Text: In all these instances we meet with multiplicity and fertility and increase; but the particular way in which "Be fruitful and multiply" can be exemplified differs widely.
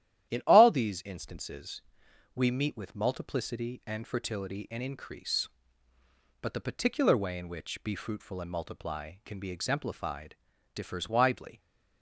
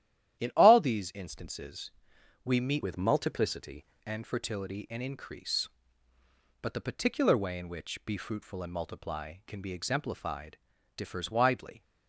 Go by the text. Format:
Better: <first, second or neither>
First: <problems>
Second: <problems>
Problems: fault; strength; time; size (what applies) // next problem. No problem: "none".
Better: first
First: starts louder than the rest; strong; until 1.3 s; 11.5 dB // pauses between "instances" and "we"; noticeable; at 1.8 s; 0.52 s long // pauses between "exemplified" and "differs"; at 10.3 s; 0.38 s long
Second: starts louder than the rest; strong; until 1.4 s; 11.5 dB // pauses between "instances" and "we"; noticeable; at 1.9 s; 0.52 s long // changes voice from "with" to "multiplicity"; from 2.8 to 3.8 s; 1.0 s long // pauses between "exemplified" and "differs"; at 10.5 s; 0.38 s long